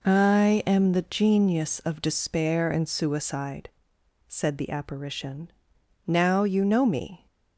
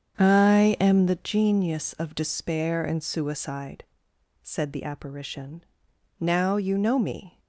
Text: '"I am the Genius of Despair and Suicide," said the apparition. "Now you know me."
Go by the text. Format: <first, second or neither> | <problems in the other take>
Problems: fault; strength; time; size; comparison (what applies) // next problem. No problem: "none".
first | starts louder than the rest; strong; until 1.2 s; 7.5 dB